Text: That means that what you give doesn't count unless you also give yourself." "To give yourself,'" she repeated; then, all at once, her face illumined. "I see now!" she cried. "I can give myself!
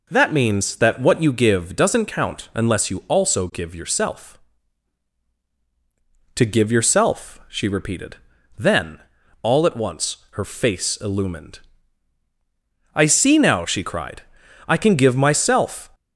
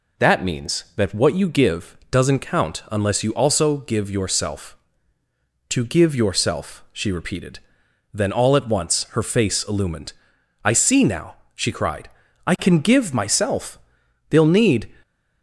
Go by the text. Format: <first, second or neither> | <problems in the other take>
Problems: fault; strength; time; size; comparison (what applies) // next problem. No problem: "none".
first | goes on to say "They'll need"; from 14.2 s on; 0.60 s long